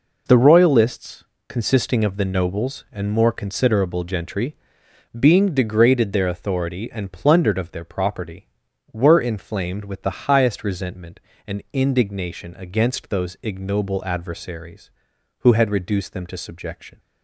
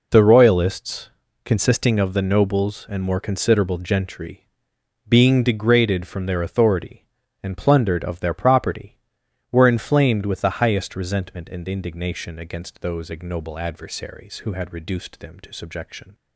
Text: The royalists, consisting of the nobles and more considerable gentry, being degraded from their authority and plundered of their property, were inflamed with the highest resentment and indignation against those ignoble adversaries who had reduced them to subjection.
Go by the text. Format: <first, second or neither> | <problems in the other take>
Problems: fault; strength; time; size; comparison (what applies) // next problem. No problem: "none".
second | skips "from"; at 6.1 s